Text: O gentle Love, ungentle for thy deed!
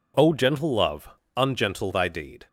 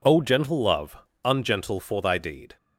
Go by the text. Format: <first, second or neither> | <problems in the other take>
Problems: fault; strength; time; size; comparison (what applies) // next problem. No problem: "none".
second | skips "for"; at 1.9 s